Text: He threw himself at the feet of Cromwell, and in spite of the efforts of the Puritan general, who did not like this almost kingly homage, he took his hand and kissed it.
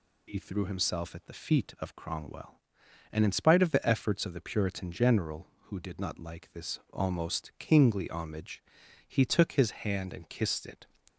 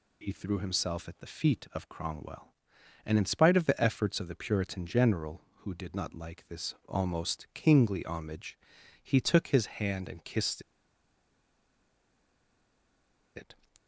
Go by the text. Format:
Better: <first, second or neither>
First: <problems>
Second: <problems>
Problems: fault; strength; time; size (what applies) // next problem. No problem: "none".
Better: first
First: none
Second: pauses between "kissed" and "it"; strong; at 10.6 s; 2.7 s long